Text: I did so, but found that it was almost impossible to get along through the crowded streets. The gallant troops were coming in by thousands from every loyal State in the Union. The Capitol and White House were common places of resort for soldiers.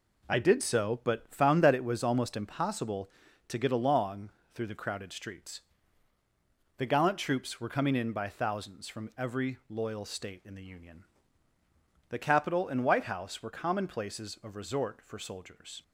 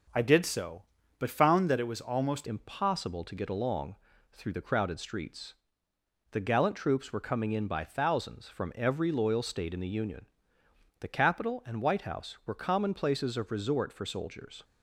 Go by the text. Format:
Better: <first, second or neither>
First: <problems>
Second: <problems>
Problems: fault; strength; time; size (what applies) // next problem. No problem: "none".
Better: first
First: pauses between "along" and "through"; slight; at 4.2 s; 0.24 s long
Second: starts louder than the rest; noticeable; until 1.5 s; 6 dB // changes voice at "impossible"; from 2.4 s on; 12.2 s long // pauses between "along" and "through"; slight; at 3.9 s; 0.36 s long